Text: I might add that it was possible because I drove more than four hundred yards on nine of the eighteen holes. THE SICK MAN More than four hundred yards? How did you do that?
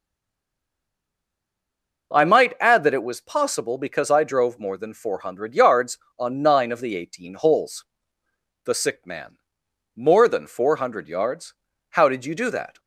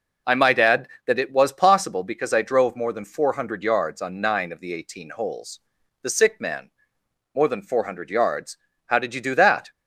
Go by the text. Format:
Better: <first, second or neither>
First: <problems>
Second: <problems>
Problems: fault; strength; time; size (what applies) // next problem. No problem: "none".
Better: second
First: stays silent before the first word; noticeable; until 2.1 s; 2.1 s long // pauses between "MAN" and "More"; noticeable; at 9.3 s; 0.58 s long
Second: pauses between "MAN" and "More"; noticeable; at 6.7 s; 0.64 s long